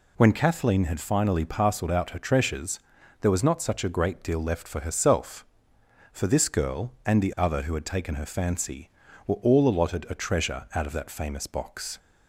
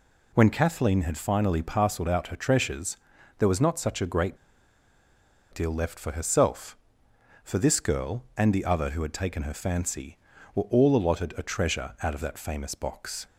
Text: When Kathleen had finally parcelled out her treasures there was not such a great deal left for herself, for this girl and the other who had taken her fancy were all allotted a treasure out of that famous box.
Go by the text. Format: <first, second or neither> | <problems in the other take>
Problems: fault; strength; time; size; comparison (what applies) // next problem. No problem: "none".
first | pauses between "treasures" and "there"; at 2.9 s; 0.40 s long; also in the first // pauses between "great" and "deal"; at 4.3 s; 1.1 s long